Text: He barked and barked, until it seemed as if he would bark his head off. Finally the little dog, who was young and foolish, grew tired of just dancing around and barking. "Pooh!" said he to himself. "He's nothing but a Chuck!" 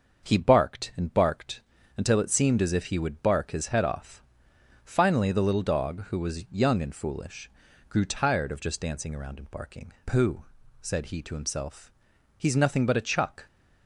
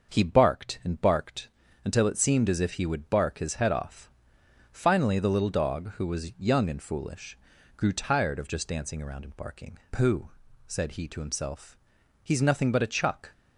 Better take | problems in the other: neither | starts louder than the rest; the same in both

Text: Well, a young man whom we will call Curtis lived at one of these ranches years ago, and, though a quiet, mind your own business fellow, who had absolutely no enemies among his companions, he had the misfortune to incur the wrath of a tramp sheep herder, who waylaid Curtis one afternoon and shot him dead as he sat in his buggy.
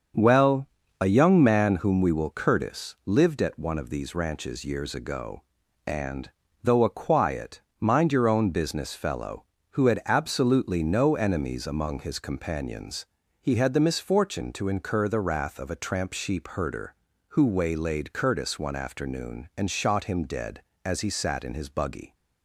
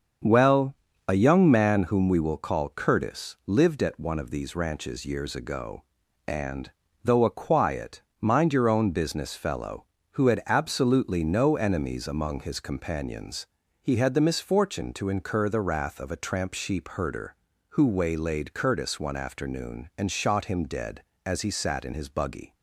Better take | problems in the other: second | starts louder than the rest; until 1.5 s; 7 dB; also in the second // skips "call"; at 2.2 s

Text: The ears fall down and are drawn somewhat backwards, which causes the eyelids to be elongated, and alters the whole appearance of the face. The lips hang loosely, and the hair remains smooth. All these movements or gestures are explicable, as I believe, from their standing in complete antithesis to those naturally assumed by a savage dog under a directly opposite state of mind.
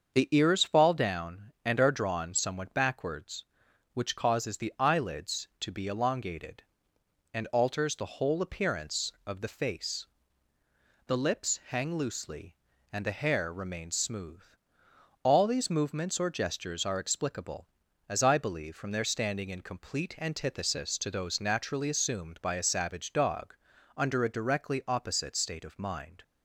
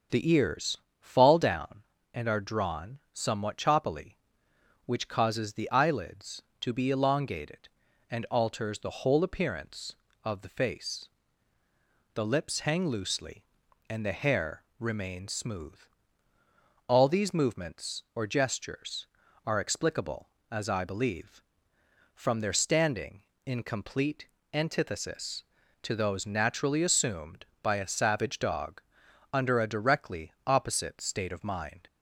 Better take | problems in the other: first | starts louder than the rest; until 1.3 s; 7 dB; also in the first // pauses between "ears" and "fall"; slight; at 0.7 s; 0.24 s long // says "choppily" for "backwards"; at 3.5 s // pauses between "hair" and "remains"; slight; at 14.6 s; 0.18 s long // pauses between "complete" and "antithesis"; slight; at 24.2 s; 0.26 s long // pauses between "dog" and "under"; noticeable; at 28.8 s; 0.52 s long; also in the first // pauses between "directly" and "opposite"; slight; at 30.3 s; 0.16 s long

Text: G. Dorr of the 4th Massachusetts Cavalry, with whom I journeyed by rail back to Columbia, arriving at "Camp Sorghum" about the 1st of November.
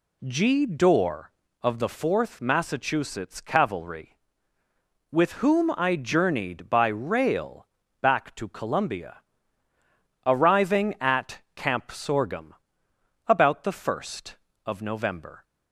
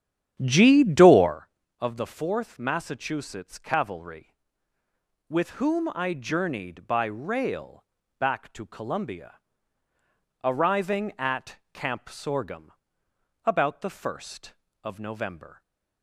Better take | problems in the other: first | starts louder than the rest; strong; until 1.5 s; 9.5 dB // pauses between "rail" and "back"; slight; at 7.8 s; 0.34 s long; slight in the first // pauses between "Sorghum" and "about"; noticeable; at 12.7 s; 0.72 s long; noticeable in the first

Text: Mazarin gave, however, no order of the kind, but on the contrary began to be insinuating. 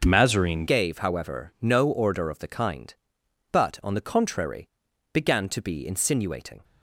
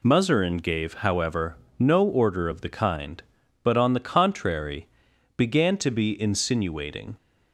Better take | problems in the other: second | starts louder than the rest; until 1.0 s; 6.5 dB // changes voice at "gave"; from 0.6 s on; 6.0 s long // pauses between "contrary" and "began"; at 4.6 s; 0.42 s long; noticeable in the second

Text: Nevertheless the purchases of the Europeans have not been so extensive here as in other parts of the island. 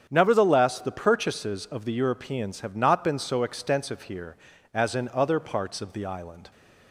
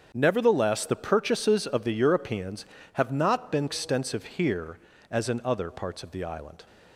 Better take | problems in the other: first | starts louder than the rest; strong; until 1.1 s; 7.5 dB; strong in the first // skips "so"; at 3.6 s

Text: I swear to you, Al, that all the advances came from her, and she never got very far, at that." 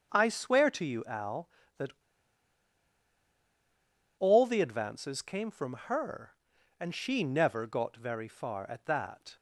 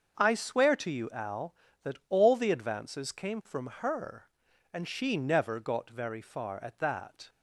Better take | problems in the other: second | starts louder than the rest; until 1.1 s; 6.5 dB; also in the second // pauses between "that" and "all"; strong; at 1.9 s; 2.2 s long

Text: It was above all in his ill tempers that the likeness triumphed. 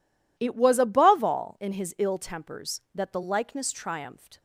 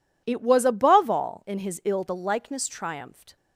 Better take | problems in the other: first | skips "tempers that"; at 2.0 s

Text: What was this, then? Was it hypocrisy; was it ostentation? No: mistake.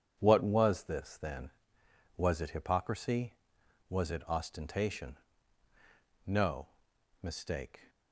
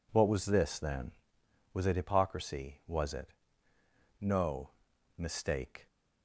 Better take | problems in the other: first | skips "ostentation"; at 3.7 s

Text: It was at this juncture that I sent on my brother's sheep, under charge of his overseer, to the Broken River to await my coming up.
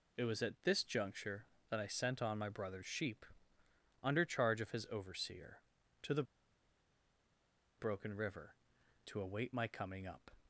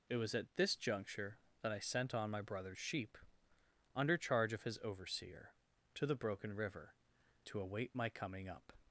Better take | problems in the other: second | pauses between "the" and "Broken"; strong; at 6.2 s; 1.5 s long

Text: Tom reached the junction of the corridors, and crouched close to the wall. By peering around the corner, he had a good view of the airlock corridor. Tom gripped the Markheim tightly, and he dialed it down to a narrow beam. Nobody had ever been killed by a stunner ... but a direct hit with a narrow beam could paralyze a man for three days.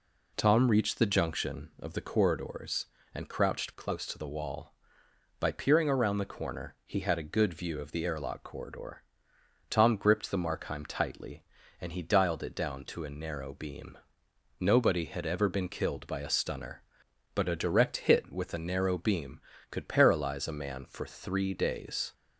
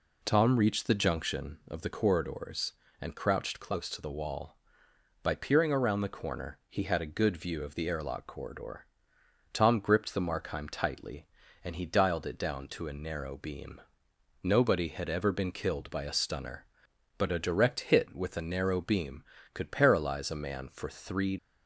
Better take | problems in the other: first | stops before "days"; at 21.3 s

